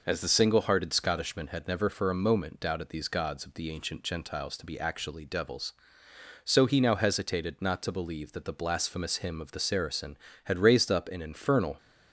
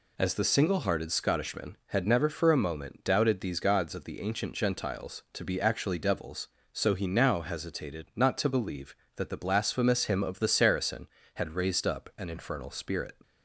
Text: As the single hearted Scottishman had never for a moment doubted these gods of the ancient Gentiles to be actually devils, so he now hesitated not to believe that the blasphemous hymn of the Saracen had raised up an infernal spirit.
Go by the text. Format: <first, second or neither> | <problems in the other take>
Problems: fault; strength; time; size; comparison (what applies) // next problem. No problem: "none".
second | stops before "spirit"; at 11.7 s